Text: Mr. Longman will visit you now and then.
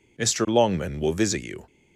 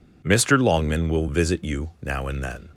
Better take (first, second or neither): second